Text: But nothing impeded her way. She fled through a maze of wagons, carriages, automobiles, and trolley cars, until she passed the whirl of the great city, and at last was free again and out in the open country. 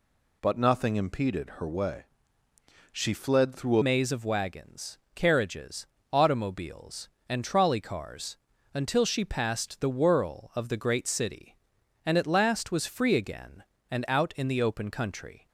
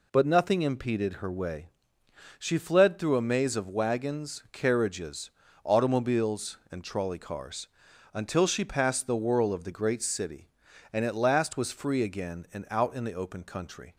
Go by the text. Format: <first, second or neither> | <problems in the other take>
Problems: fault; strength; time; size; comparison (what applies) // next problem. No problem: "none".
second | changes voice at "maze"; from 3.8 s on; 11.6 s long